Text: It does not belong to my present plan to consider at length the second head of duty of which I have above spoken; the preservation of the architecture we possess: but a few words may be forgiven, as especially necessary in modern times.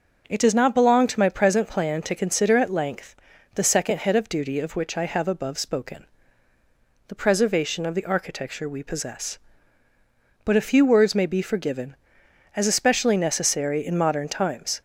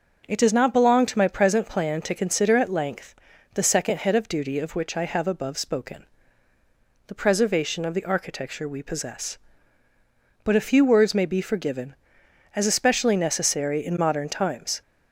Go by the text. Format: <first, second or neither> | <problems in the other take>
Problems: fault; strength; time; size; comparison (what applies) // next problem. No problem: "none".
neither | starts louder than the rest; the same in both // pauses between "length" and "the"; the same in both